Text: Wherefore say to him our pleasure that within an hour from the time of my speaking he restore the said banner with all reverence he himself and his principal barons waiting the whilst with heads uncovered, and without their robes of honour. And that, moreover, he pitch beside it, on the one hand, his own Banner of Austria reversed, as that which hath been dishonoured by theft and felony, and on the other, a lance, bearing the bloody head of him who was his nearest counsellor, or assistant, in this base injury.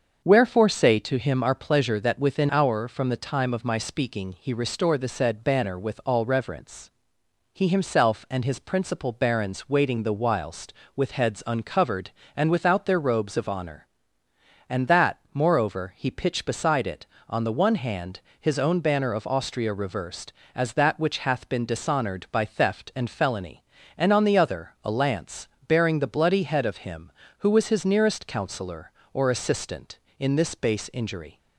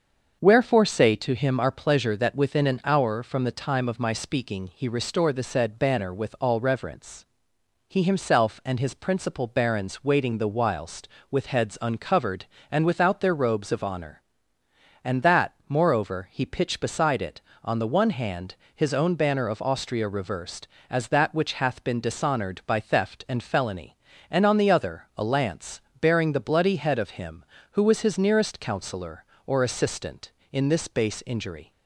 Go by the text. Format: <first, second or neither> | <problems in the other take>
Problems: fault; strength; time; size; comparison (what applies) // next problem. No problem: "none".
second | starts louder than the rest; until 1.2 s; 6.5 dB; also in the second // skips "an"; at 2.4 s // pauses between "reverence" and "he"; noticeable; at 6.8 s; 0.64 s long; noticeable in the second